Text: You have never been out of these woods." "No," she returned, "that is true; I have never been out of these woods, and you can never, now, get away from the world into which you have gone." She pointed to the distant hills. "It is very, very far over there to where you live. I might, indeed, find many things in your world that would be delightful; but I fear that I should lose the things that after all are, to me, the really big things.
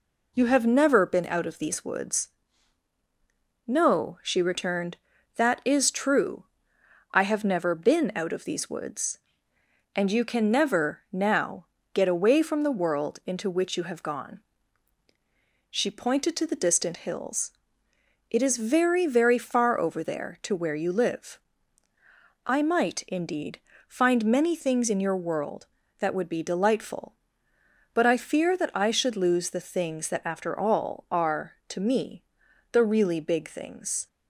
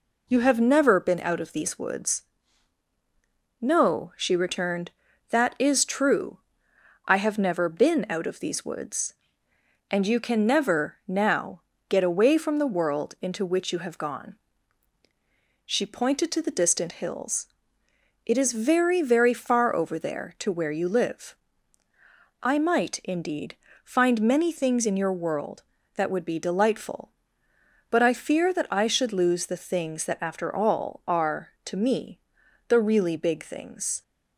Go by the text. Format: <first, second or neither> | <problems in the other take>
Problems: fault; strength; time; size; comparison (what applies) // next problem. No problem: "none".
neither | none